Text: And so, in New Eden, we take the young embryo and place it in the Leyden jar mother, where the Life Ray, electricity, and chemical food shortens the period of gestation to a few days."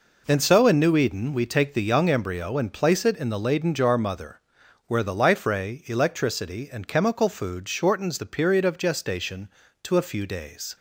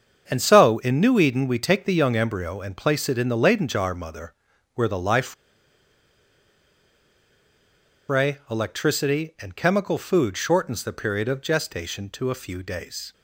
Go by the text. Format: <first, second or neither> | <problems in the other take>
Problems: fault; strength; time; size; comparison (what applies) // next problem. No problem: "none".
first | starts louder than the rest; until 1.2 s; 7 dB // pauses between "Life" and "Ray"; strong; at 5.3 s; 2.7 s long